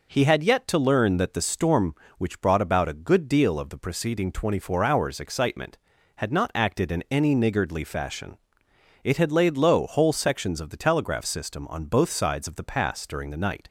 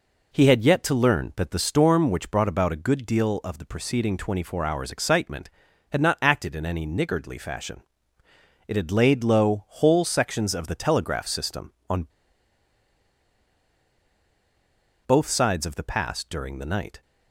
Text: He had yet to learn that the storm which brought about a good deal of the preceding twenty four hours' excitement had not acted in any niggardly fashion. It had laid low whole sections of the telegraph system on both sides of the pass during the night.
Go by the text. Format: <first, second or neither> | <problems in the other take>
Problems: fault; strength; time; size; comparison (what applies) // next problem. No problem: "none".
first | pauses between "on" and "both"; strong; at 12.0 s; 3.0 s long